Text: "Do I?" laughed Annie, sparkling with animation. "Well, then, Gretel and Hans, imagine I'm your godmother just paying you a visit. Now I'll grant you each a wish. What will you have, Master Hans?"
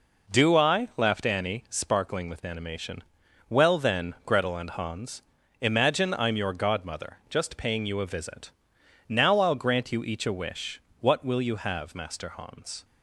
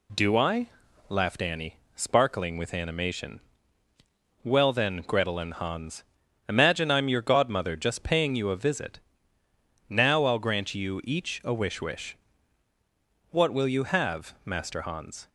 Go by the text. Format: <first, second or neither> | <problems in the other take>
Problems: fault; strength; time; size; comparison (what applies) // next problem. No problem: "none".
first | says "wish" twice; at 11.8 s